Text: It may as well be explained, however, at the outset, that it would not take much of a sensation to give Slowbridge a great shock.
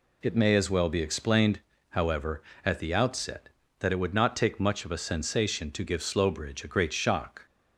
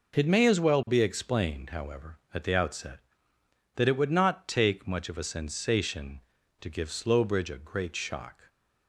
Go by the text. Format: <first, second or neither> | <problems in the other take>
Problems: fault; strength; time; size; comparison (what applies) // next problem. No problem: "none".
neither | none